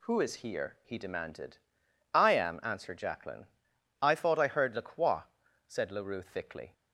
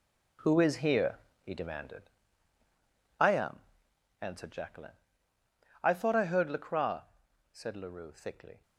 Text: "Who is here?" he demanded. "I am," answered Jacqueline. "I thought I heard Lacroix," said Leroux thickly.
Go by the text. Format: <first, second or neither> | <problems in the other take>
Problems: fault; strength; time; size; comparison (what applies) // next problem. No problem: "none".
first | gets quieter; strong; throughout; 10 dB